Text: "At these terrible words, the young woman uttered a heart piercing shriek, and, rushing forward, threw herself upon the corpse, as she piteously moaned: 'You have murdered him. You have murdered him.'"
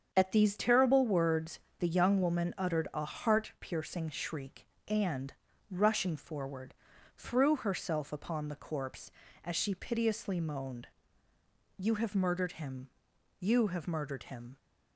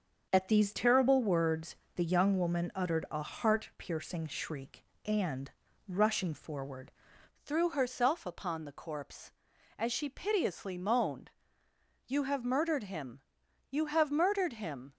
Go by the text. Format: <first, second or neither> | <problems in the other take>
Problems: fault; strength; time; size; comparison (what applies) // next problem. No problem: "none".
first | starts louder than the rest; until 1.3 s; 6.5 dB; strong in the first // changes voice at "threw"; from 7.4 s on; 7.5 s long